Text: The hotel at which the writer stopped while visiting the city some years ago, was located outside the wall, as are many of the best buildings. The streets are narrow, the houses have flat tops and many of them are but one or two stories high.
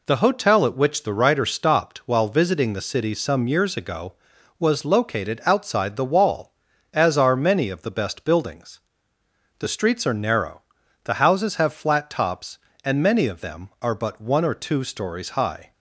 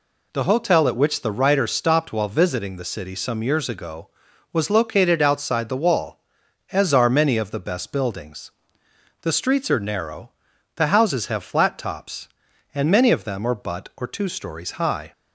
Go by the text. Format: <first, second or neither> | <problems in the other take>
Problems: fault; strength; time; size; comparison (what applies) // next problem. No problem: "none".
first | skips "one"; at 13.9 s